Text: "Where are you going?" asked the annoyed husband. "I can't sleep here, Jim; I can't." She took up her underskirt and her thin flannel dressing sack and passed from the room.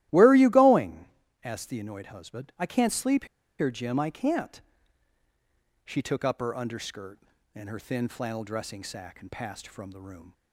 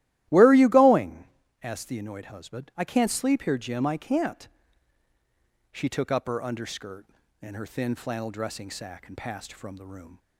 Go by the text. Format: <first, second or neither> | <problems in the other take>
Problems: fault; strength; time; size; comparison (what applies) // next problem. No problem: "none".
second | starts louder than the rest; strong; until 1.4 s; 14.5 dB; strong in the second // pauses between "sleep" and "here"; slight; at 3.2 s; 0.33 s long